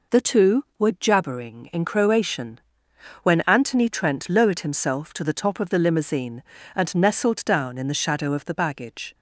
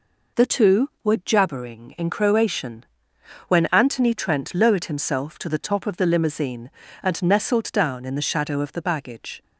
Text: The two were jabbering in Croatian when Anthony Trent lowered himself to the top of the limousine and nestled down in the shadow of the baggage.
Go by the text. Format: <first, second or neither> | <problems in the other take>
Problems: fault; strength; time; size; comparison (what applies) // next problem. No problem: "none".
neither | pauses between "Croatian" and "when"; noticeable; the same in both